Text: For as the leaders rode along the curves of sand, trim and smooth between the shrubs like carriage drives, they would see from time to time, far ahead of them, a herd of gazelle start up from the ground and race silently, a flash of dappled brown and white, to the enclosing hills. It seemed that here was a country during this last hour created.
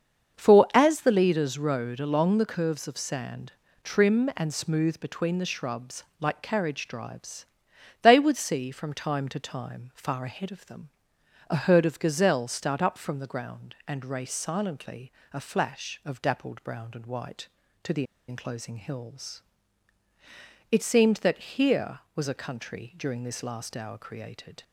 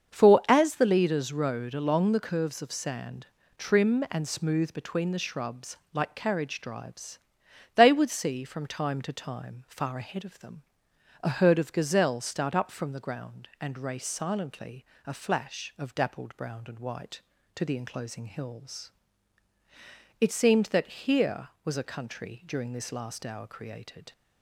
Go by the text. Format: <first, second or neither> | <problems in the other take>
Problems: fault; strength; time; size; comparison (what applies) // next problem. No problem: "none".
second | starts louder than the rest; until 1.4 s; 7 dB; also in the second // pauses between "shrubs" and "like"; slight; at 6.0 s; 0.16 s long; slight in the second // pauses between "the" and "enclosing"; slight; at 18.0 s; 0.24 s long